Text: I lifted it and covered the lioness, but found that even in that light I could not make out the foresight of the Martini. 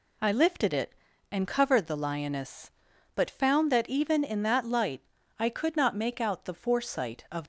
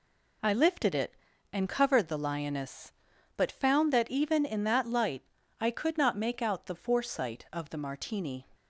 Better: second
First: pauses between "light" and "I"; at 5.0 s; 0.38 s long // stops before "the Martini"; at 7.4 s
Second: pauses between "light" and "I"; at 5.2 s; 0.38 s long

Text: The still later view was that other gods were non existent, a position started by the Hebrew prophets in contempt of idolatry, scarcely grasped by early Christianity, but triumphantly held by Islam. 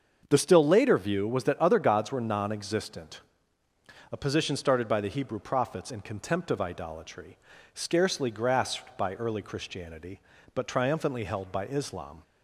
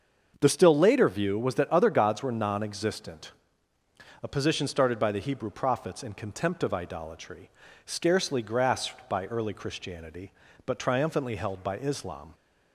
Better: neither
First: starts louder than the rest; until 1.3 s; 6.5 dB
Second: starts louder than the rest; until 1.4 s; 6.5 dB

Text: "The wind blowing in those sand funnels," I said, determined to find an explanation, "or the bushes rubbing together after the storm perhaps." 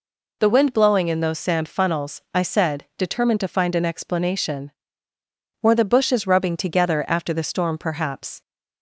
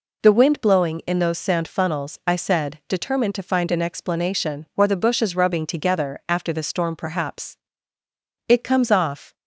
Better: first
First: none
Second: goes on to say "It comes off"; noticeable; from 8.4 s on; 0.88 s long

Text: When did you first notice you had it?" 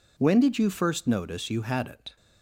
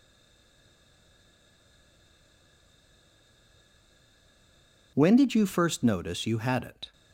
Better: first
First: none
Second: stays silent before the first word; strong; until 4.9 s; 4.9 s long

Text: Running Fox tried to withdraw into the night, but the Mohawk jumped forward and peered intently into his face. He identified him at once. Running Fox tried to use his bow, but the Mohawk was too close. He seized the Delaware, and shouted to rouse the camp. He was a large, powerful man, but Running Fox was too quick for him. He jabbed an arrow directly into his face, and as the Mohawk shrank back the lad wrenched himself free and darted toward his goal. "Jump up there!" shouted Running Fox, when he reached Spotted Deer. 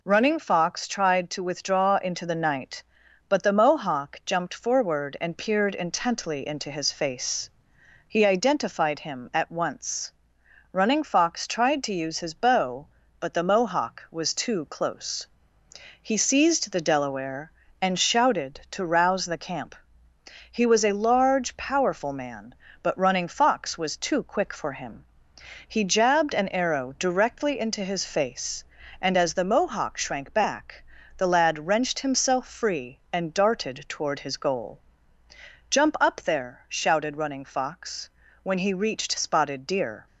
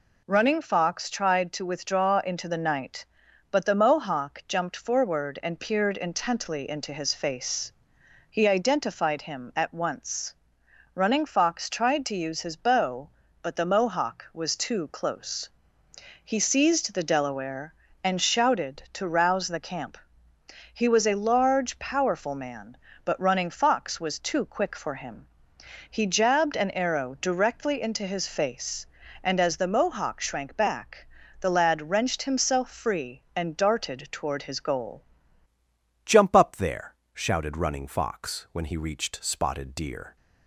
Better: first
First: pauses between "back" and "the"; slight; at 30.8 s; 0.32 s long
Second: pauses between "back" and "the"; slight; at 31.0 s; 0.32 s long // changes voice at "Jump"; from 36.0 s on; 4.1 s long

